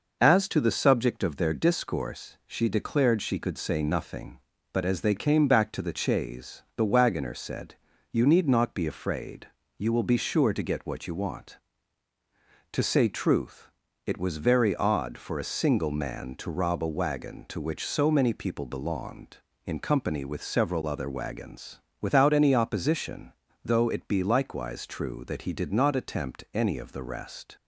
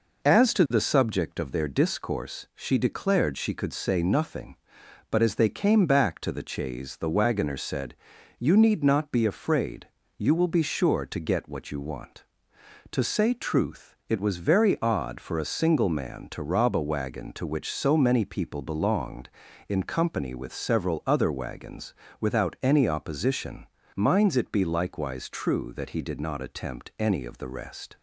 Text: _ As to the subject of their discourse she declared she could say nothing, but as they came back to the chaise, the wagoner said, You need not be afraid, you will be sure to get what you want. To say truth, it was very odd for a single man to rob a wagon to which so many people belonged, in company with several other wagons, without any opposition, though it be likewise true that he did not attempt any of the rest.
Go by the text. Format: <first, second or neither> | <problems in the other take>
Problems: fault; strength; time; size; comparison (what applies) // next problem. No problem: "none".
first | says "minds" for "though"; at 23.9 s